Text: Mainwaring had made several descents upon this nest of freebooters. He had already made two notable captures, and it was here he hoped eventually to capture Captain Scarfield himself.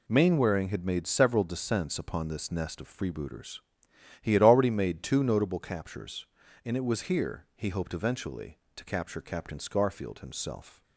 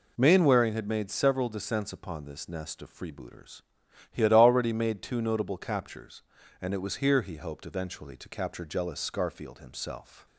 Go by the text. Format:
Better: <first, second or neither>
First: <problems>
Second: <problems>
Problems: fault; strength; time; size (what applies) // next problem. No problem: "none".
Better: first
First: none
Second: says "Jealous" for "Captain"; at 8.6 s